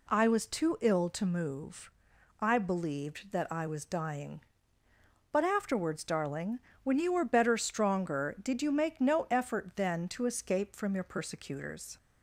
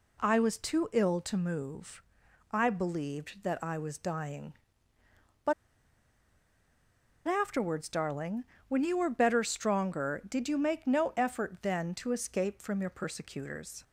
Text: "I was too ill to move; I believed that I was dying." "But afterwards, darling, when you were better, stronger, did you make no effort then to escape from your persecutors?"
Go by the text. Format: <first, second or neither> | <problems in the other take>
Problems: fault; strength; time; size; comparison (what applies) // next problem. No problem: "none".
first | pauses between "But" and "afterwards"; strong; at 5.5 s; 1.7 s long